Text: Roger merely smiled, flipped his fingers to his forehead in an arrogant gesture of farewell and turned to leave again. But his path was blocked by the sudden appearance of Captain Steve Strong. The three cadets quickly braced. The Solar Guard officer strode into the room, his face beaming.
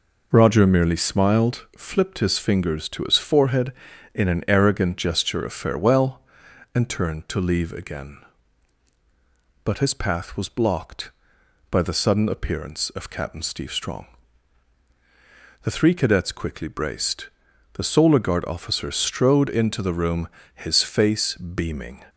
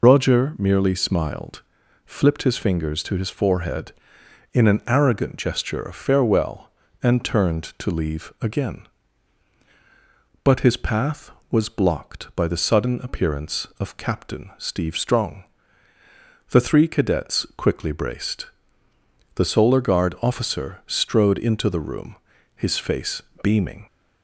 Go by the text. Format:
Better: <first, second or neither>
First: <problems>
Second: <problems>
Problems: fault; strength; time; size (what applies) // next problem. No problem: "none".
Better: first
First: none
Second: loses the start of "Roger"; at 0.0 s; 70 ms // pauses between "face" and "beaming"; slight; at 23.2 s; 0.22 s long